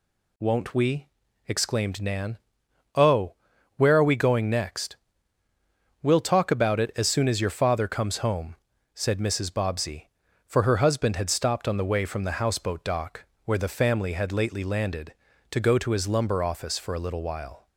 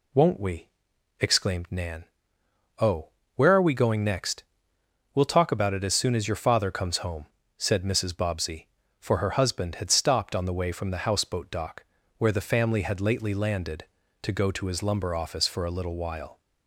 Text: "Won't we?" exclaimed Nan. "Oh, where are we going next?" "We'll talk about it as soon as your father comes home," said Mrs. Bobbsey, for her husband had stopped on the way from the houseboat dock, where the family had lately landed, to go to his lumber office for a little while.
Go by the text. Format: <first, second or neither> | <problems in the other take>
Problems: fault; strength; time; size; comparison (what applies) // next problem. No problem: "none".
neither | none